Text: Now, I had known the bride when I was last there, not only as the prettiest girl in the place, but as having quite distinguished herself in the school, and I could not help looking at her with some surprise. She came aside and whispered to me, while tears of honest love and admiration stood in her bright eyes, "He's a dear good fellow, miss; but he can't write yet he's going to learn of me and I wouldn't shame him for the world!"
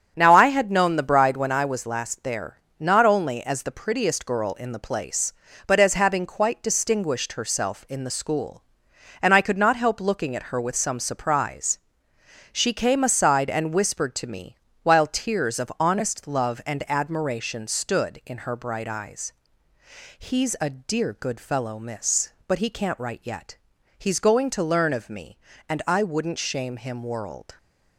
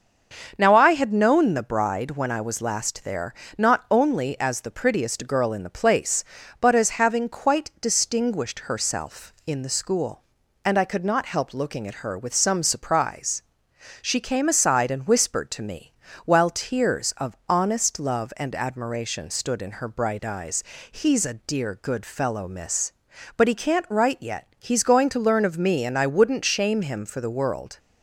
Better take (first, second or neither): second